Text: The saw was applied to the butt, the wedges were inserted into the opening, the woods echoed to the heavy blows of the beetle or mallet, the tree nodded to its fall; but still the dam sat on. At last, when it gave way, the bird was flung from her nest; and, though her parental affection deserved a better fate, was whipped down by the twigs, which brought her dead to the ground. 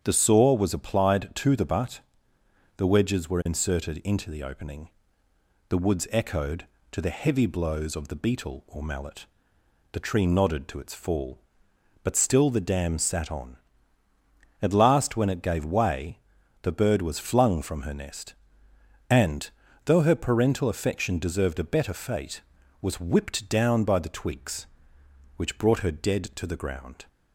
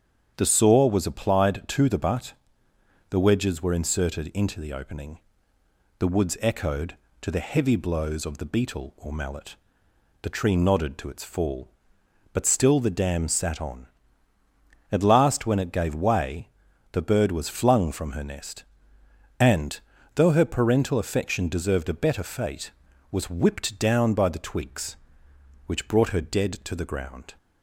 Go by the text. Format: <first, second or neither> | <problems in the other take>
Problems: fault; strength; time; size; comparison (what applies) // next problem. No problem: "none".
neither | starts louder than the rest; strong; the same in both